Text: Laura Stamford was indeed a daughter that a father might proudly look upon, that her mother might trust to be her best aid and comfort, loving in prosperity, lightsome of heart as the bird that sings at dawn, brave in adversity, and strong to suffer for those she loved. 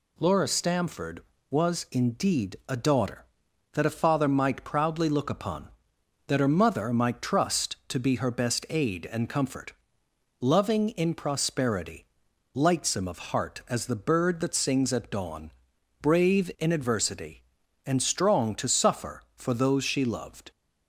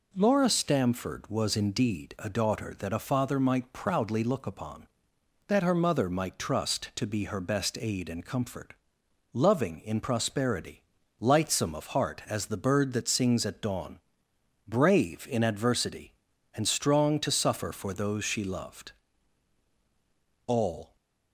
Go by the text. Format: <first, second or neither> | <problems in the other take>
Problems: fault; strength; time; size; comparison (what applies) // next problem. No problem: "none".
first | goes on to say "All"; slight; from 20.4 s on; 0.48 s long